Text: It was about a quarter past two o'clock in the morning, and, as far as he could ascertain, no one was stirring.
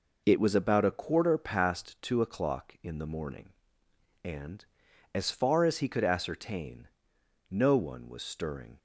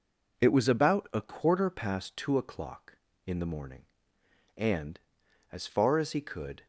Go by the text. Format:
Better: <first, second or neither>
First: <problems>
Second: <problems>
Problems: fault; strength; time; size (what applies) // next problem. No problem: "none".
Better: first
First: none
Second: stops before "ascertain no one was stirring"; at 6.6 s